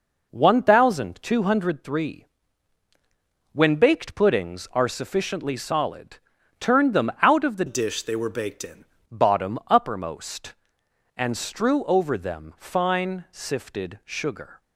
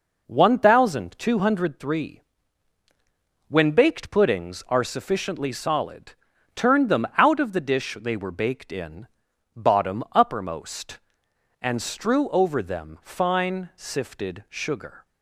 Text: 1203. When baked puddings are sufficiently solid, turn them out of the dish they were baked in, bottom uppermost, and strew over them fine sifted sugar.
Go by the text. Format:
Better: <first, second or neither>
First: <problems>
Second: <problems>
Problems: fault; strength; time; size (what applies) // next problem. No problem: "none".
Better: second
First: changes voice from "dish" to "in"; from 7.6 to 8.8 s; 1.2 s long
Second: none